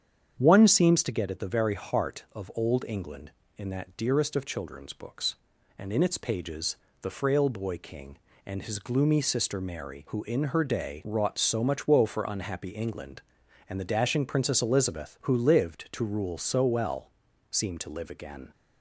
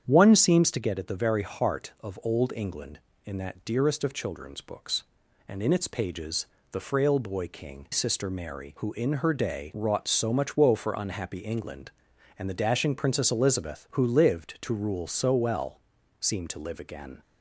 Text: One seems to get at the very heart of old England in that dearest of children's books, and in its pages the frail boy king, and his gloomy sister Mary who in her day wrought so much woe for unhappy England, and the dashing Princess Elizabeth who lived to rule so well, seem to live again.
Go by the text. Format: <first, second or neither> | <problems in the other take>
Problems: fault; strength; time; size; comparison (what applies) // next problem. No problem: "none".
first | starts louder than the rest; strong; until 1.0 s; 8.5 dB; strong in the first // pauses between "pages" and "the"; slight; at 6.4 s; 0.24 s long; slight in the first // skips "and his gloomy"; at 7.8 s